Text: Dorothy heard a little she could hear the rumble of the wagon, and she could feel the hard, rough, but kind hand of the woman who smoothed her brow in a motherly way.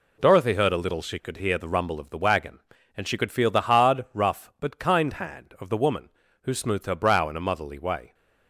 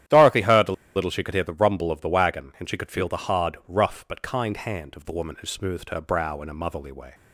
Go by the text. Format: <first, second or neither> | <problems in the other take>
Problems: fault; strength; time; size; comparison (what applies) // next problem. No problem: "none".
first | starts louder than the rest; strong; until 1.3 s; 11 dB // pauses between "a" and "little"; slight; at 0.7 s; 0.23 s long